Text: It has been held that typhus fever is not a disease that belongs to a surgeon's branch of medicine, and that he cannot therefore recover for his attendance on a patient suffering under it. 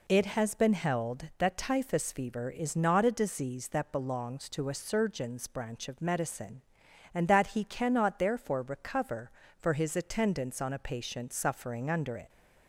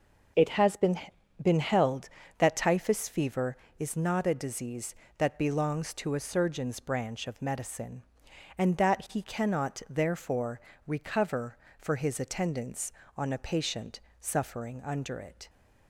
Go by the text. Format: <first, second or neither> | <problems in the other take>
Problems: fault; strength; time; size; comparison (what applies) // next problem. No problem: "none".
first | says "been" twice; at 1.4 s // pauses between "therefore" and "recover"; slight; at 10.5 s; 0.26 s long // pauses between "patient" and "suffering"; slight; at 13.9 s; 0.20 s long